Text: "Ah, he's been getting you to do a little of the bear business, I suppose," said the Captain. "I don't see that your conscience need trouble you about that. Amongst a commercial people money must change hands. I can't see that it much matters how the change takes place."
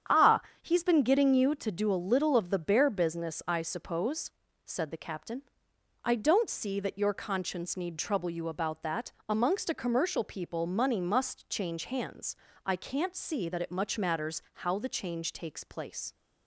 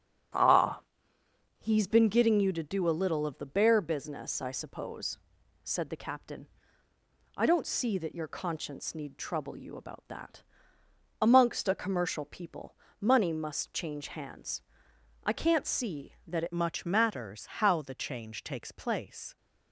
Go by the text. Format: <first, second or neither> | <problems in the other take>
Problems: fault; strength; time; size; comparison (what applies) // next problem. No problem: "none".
first | starts louder than the rest; strong; until 2.1 s; 8 dB; strong in the first // pauses between "people" and "money"; slight; at 12.7 s; 0.24 s long // changes voice at "much"; from 16.5 s on; 2.8 s long // pauses between "matters" and "how"; slight; at 17.4 s; 0.16 s long